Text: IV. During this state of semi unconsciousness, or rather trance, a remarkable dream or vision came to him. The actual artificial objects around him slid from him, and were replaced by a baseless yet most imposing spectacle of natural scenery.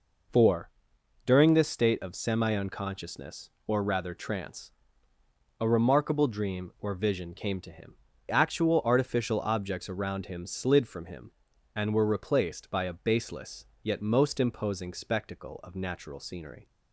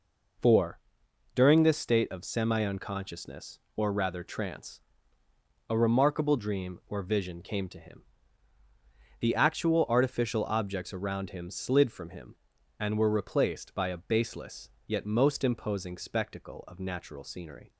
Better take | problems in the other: second | skips "The"; at 8.1 s // pauses between "baseless" and "yet"; slight; at 13.6 s; 0.16 s long; slight in the second

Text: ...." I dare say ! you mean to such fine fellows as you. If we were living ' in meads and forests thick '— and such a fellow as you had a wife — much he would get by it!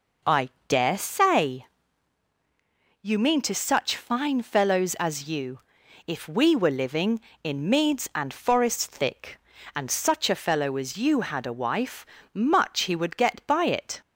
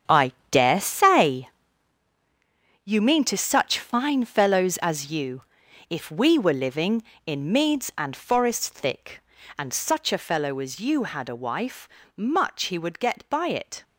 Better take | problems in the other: first | gets quieter; strong; throughout; 11.5 dB // pauses between "I" and "dare"; slight; at 0.3 s; 0.18 s long; slight in the first

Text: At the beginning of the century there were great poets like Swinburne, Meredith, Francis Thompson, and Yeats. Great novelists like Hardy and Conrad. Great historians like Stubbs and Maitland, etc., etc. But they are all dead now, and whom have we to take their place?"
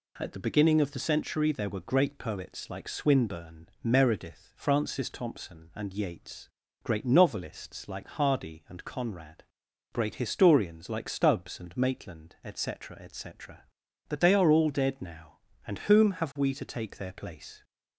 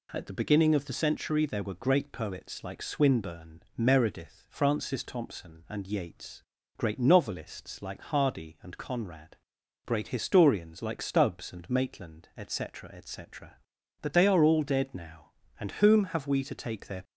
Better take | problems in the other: first | stops before "place"; at 17.0 s

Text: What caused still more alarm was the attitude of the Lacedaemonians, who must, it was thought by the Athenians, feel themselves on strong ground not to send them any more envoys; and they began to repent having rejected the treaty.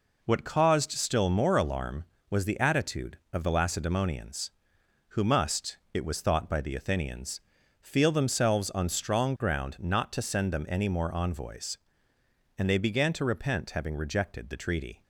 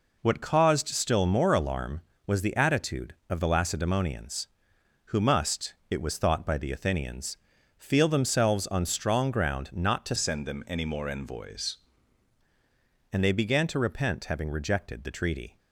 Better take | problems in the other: first | changes voice from "send" to "envoys"; from 10.1 to 11.7 s; 1.6 s long

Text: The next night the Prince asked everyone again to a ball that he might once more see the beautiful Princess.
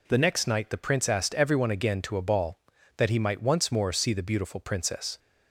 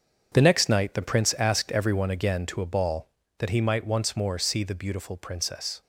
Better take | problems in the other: first | gets quieter; strong; throughout; 10.5 dB

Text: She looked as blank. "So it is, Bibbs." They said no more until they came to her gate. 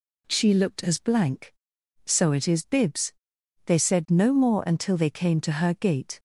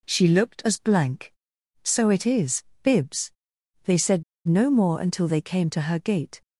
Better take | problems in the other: first | pauses between "said" and "no"; slight; at 4.2 s; 0.23 s long

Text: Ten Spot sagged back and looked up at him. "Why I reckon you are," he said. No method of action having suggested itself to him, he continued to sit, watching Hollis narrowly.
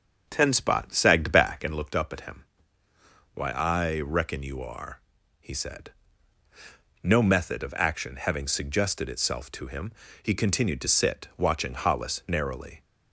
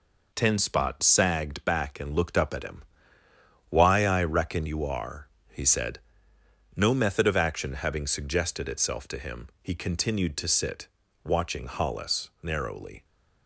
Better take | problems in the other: second | starts louder than the rest; until 2.0 s; 6.5 dB

